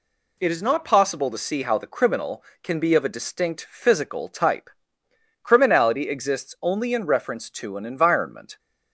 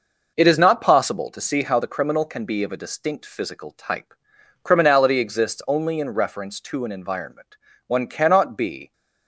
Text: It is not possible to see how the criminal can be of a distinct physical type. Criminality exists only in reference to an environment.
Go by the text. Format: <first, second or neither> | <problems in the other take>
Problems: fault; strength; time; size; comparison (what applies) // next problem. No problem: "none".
first | goes on to say "One cannot be"; noticeable; from 7.8 s on; 1.0 s long